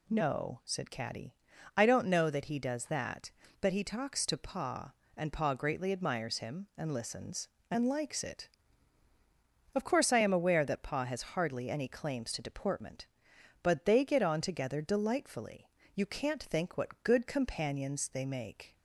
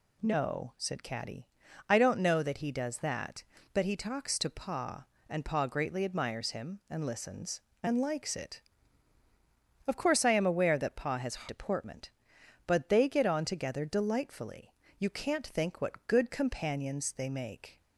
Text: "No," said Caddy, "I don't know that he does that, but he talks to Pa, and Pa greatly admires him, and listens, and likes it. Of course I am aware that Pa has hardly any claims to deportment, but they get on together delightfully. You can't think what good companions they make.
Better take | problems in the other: first | skips "hardly any claims to"; at 11.4 s

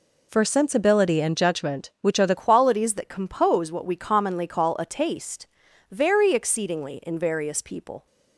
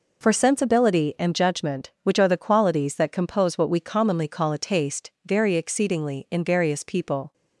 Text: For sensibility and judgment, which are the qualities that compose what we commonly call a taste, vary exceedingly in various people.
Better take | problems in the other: second | changes voice at "qualities"; from 2.3 s on; 5.7 s long

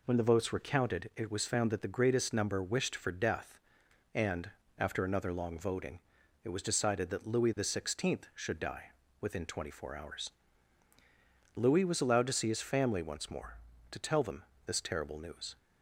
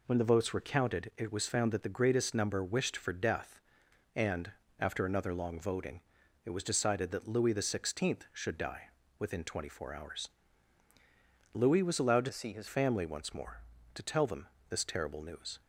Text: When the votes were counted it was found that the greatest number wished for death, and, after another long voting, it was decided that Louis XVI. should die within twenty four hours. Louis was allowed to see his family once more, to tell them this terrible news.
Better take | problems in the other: first | pauses between "die" and "within"; slight; at 8.8 s; 0.28 s long; slight in the first // changes voice from "see" to "his"; from 12.3 to 12.6 s; 0.3 s long // pauses between "them" and "this"; slight; at 14.4 s; 0.22 s long; slight in the first

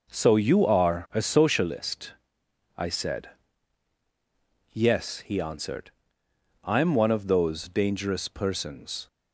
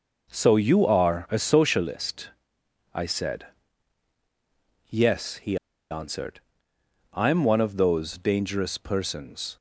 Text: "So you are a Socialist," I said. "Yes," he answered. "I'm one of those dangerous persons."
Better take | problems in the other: first | pauses between "he" and "answered"; slight; at 5.5 s; 0.34 s long

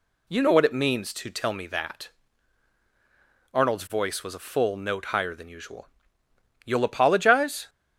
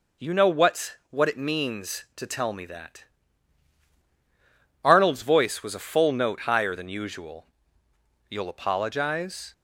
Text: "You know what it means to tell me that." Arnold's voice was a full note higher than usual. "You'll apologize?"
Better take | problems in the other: first | says "what" twice; at 1.0 s

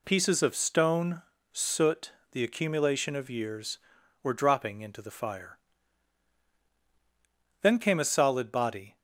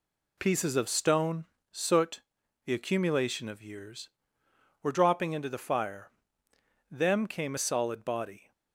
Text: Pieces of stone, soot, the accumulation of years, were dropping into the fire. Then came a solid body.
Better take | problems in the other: first | says "Them" for "Then"; at 6.8 s

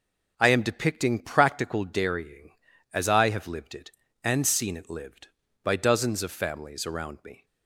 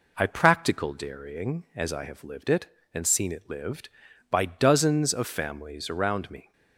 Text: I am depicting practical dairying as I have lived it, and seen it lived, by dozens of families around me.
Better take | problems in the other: first | skips "am depicting"; at 0.2 s

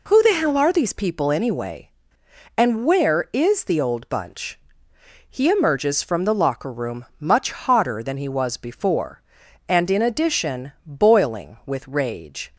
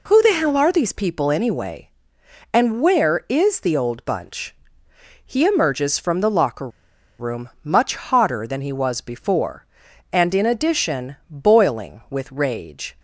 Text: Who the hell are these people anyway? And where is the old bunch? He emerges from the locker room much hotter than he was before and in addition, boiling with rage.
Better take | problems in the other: first | pauses between "locker" and "room"; noticeable; at 6.6 s; 0.50 s long // pauses between "room" and "much"; slight; at 7.4 s; 0.16 s long; slight in the first

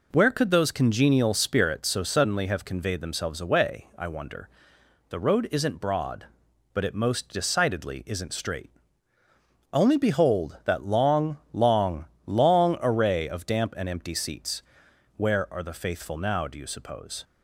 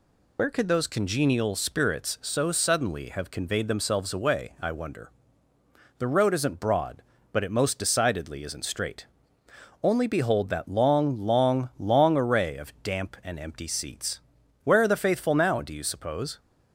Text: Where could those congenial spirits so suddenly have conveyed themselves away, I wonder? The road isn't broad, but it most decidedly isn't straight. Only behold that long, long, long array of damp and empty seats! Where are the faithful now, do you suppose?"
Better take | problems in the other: first | loses the start of "Where"; at 0.3 s; 80 ms

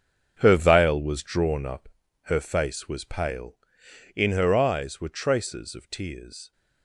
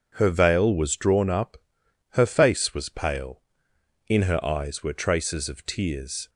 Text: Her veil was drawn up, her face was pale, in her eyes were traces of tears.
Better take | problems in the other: second | gets quieter; strong; throughout; 12 dB

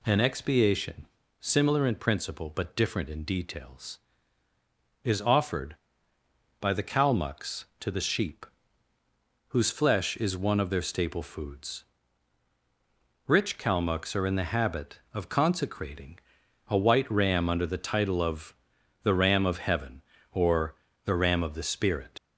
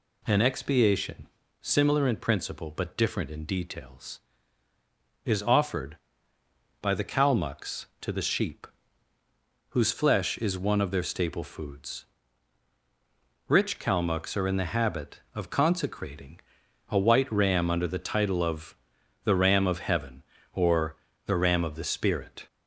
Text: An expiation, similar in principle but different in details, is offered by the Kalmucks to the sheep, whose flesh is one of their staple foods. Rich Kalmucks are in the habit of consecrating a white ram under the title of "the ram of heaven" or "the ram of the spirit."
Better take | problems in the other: second | pauses between "consecrating" and "a"; noticeable; at 16.1 s; 0.50 s long; noticeable in the second // pauses between "of" and "the"; noticeable; at 18.5 s; 0.48 s long; noticeable in the second // pauses between "or" and "the"; slight; at 20.7 s; 0.32 s long; slight in the second // leaves "spirit" unfinished; at 22.1 s; 75 ms

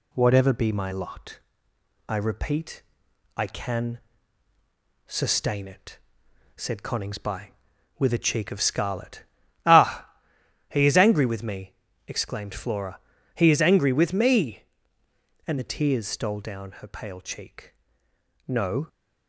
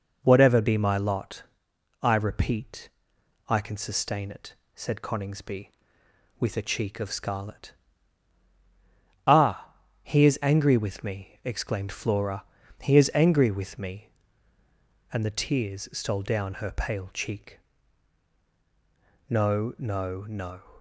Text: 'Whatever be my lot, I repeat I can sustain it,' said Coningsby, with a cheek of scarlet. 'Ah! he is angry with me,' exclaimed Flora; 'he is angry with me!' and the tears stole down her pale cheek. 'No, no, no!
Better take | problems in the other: second | pauses between "repeat" and "I"; noticeable; at 2.8 s; 0.54 s long; noticeable in the second // pauses between "can" and "sustain"; at 3.9 s; 1.0 s long // stops before "no no"; at 18.8 s

